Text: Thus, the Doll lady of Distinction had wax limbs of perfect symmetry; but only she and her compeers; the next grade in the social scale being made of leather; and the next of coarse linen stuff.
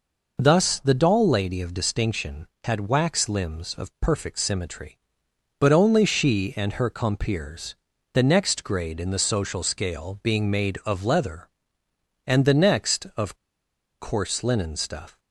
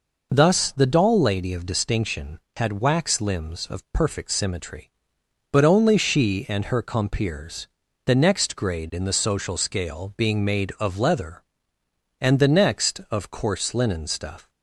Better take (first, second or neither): second